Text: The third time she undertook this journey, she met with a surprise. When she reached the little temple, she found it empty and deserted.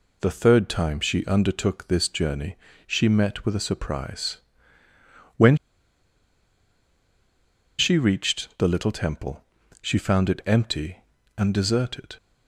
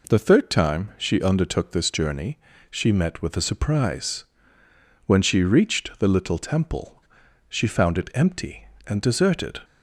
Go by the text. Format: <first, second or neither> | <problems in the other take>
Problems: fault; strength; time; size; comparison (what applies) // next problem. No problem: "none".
second | pauses between "When" and "she"; strong; at 5.5 s; 2.2 s long